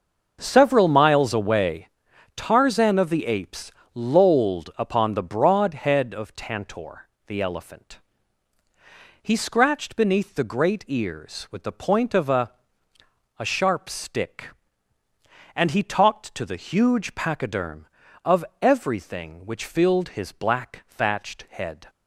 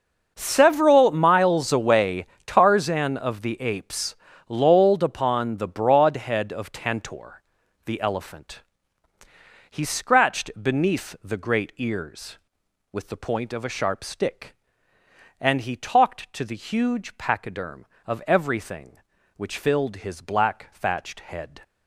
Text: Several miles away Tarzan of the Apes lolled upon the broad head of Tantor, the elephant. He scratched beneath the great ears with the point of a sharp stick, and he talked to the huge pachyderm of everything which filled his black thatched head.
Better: second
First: starts louder than the rest; until 1.4 s; 6 dB // pauses between "away" and "Tarzan"; noticeable; at 1.8 s; 0.48 s long // pauses between "Apes" and "lolled"; slight; at 3.7 s; 0.22 s long // says "a" twice; at 13.3 s // pauses between "of" and "everything"; slight; at 18.4 s; 0.16 s long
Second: starts louder than the rest; until 1.3 s; 6 dB // pauses between "away" and "Tarzan"; slight; at 2.2 s; 0.20 s long // pauses between "Apes" and "lolled"; slight; at 4.1 s; 0.32 s long

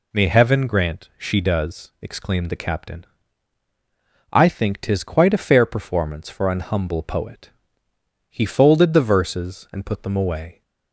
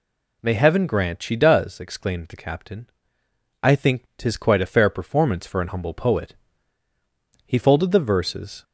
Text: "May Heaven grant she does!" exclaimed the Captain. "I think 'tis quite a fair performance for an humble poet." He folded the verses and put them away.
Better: first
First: none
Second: stops before "and put them away"; at 8.6 s

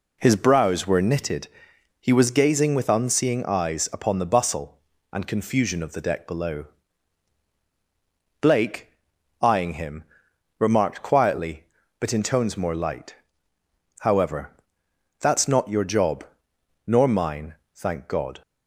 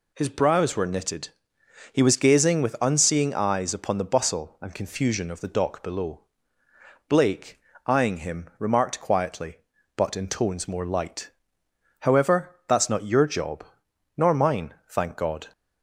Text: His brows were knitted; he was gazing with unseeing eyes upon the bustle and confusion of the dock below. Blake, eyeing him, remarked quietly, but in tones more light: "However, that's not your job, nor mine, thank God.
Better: second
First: says "deck" for "dock"; at 6.0 s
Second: none

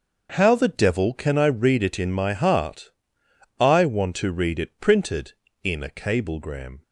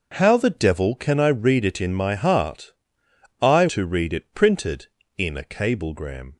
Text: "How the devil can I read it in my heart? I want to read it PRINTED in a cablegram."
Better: first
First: starts louder than the rest; until 1.3 s; 6.5 dB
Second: starts louder than the rest; noticeable; until 1.1 s; 6 dB // skips "want"; at 3.6 s

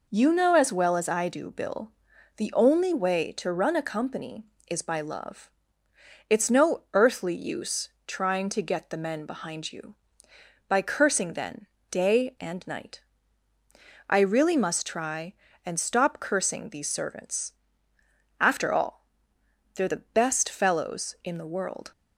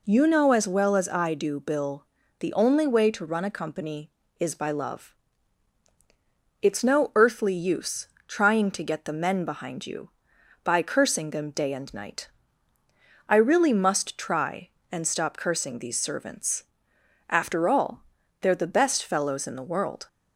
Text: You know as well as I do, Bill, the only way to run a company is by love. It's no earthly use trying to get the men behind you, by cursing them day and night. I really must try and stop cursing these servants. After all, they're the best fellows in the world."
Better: second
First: pauses between "use" and "trying"; slight; at 7.8 s; 0.16 s long // says "then" for "them"; at 11.3 s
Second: pauses between "use" and "trying"; slight; at 8.0 s; 0.20 s long

